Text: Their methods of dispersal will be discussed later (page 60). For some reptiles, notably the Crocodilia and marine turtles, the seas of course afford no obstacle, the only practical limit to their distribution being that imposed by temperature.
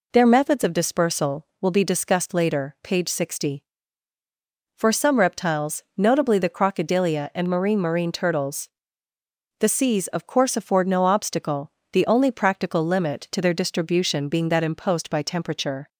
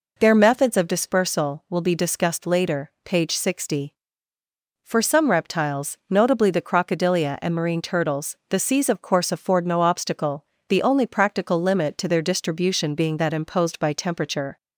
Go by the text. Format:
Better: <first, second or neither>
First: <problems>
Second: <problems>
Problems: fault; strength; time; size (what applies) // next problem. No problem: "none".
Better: second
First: says "marine" twice; at 7.8 s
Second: none